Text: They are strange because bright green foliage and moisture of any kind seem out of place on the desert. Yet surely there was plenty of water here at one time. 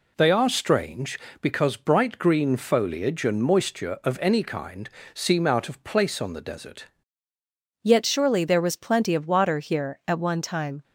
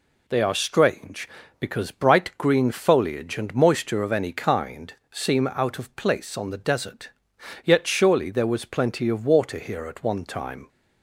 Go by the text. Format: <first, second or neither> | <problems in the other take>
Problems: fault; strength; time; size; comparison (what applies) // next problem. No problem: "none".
second | pauses between "kind" and "seem"; slight; at 4.8 s; 0.24 s long; slight in the second // changes voice at "Yet"; from 7.8 s on; 3.0 s long